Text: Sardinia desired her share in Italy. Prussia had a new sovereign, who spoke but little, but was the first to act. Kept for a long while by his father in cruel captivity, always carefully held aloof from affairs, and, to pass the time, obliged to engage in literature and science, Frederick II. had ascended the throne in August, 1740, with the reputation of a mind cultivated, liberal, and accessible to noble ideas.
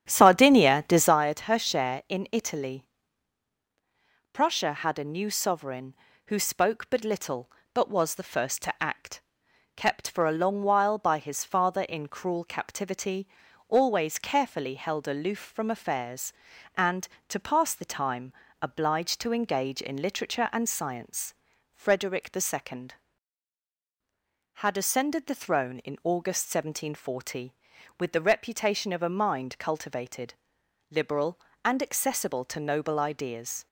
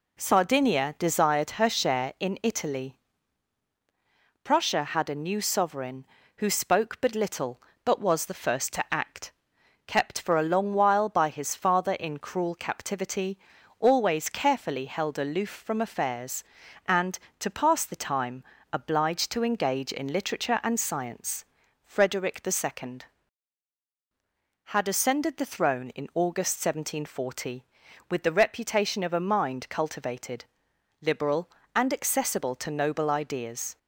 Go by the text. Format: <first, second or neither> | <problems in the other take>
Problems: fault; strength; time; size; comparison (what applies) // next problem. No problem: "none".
second | starts louder than the rest; strong; until 1.2 s; 9.5 dB